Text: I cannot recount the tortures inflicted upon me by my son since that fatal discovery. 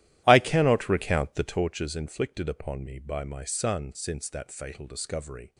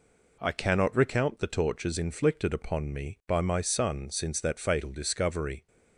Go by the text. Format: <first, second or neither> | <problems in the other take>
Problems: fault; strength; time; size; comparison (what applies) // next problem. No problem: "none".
second | starts louder than the rest; strong; until 1.7 s; 13.5 dB